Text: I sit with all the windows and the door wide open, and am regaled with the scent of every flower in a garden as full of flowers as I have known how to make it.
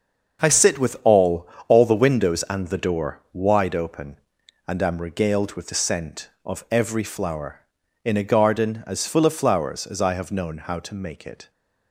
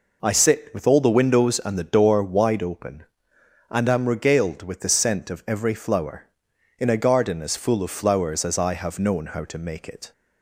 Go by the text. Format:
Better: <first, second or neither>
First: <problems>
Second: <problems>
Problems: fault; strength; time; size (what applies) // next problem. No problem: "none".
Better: second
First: starts louder than the rest; until 1.7 s; 7 dB // says "all" twice; at 1.6 s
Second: none